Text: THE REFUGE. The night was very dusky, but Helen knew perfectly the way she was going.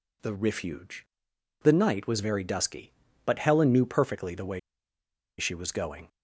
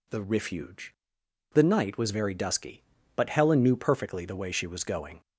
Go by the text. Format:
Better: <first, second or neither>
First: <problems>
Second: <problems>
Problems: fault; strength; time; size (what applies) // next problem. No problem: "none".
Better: second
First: pauses between "way" and "she"; noticeable; at 4.5 s; 0.78 s long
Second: none